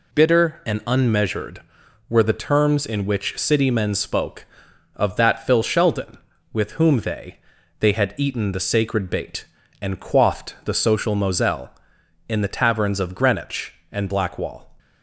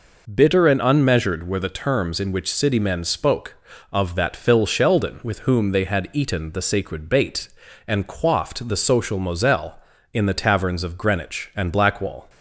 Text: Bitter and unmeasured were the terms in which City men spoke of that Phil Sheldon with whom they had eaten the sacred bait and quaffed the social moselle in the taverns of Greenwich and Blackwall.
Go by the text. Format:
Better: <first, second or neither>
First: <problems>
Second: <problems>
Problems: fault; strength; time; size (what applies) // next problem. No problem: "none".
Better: second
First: says "they" twice; at 7.7 s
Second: none